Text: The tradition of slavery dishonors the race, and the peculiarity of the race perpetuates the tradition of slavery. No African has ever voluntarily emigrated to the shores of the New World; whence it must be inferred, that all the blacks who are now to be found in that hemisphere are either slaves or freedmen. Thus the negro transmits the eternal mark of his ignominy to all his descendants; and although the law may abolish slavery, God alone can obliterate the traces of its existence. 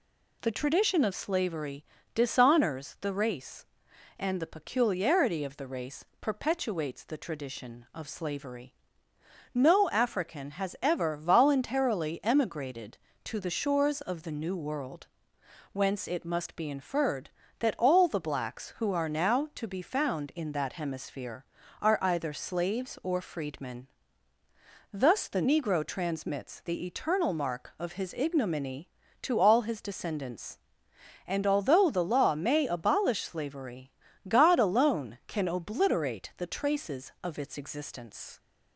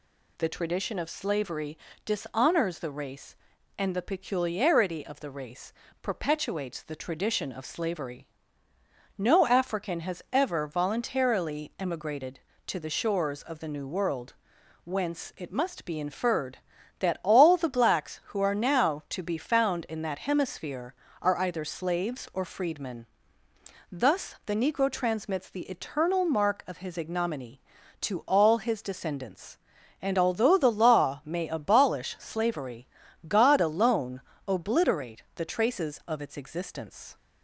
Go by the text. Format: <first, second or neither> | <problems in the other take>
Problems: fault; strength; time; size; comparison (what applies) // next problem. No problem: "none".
first | pauses between "slavery" and "dishonors"; slight; at 1.7 s; 0.28 s long; slight in the first // pauses between "race" and "perpetuates"; slight; at 5.7 s; 0.30 s long; slight in the first // skips "can"; at 34.3 s